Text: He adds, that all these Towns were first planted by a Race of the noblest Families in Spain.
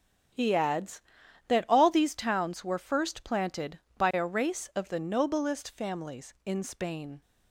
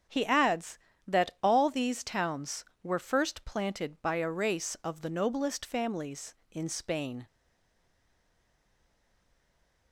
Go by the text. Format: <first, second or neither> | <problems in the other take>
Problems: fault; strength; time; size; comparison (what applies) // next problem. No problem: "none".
first | starts louder than the rest; strong; until 1.5 s; 8 dB; also in the first // stays silent after the last word; strong; from 7.2 s on; 2.7 s long